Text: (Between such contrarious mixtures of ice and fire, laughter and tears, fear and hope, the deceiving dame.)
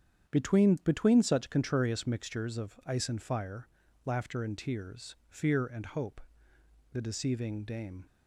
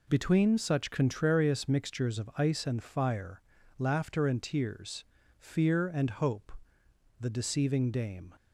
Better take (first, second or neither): second